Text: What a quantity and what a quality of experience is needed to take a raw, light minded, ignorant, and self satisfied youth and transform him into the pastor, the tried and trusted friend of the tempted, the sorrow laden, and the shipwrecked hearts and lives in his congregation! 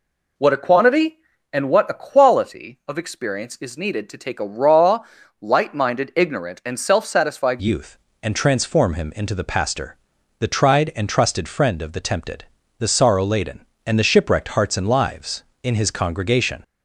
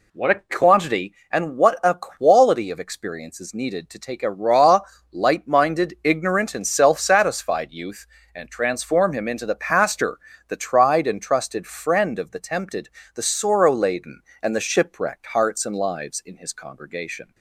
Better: second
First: changes voice at "youth"; from 7.6 s on; 9.0 s long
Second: none

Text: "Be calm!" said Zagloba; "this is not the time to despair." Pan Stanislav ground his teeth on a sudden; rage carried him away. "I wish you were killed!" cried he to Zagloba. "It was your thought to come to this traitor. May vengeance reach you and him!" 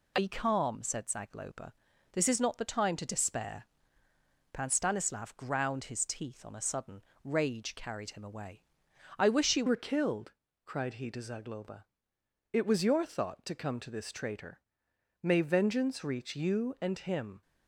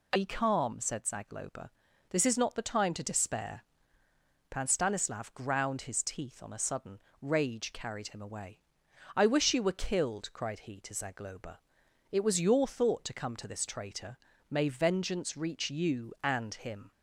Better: second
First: changes voice at "were"; from 9.6 s on; 7.8 s long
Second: none

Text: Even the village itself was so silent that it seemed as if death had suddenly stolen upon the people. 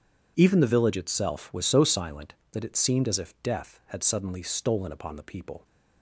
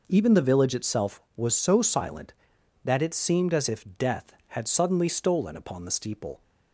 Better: first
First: none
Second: says "steeple" for "people"; at 5.9 s

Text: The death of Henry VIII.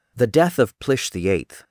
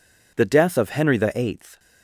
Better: second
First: says "Plish" for "Henry"; at 0.7 s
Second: none

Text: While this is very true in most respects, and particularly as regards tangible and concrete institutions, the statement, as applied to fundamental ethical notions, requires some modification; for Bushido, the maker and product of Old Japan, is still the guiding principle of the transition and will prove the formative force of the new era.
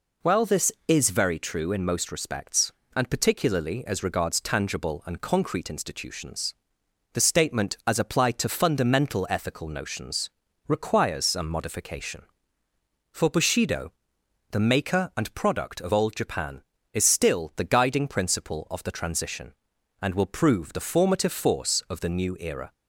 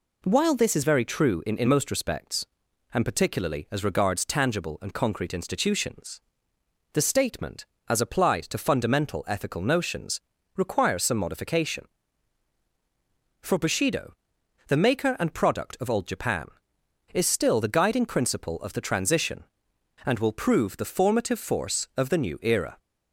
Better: first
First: none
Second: says "in" twice; at 1.5 s

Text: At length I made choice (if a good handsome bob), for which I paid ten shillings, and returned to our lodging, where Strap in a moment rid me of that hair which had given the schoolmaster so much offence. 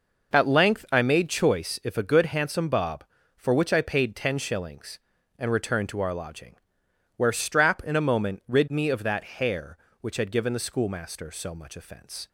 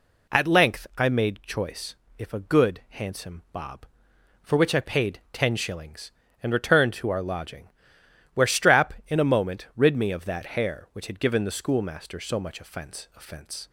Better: first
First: none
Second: says "offence" twice; at 13.1 s

